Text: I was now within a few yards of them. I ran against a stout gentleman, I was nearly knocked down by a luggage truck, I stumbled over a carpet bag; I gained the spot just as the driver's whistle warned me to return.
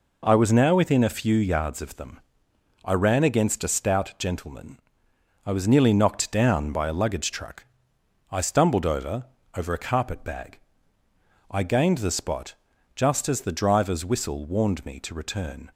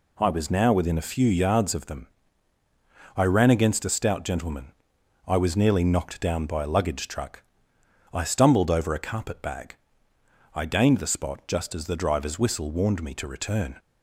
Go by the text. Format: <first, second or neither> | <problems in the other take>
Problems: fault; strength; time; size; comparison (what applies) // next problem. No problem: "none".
second | says "over" twice; at 9.5 s // pauses between "spot" and "just"; at 12.5 s; 0.42 s long